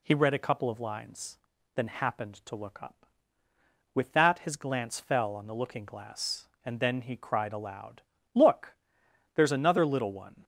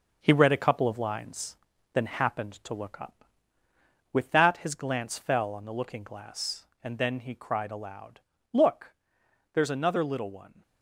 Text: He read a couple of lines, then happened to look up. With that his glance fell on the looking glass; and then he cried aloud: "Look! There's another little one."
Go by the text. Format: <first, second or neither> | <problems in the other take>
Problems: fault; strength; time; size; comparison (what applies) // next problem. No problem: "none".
first | gets quieter; noticeable; throughout; 5 dB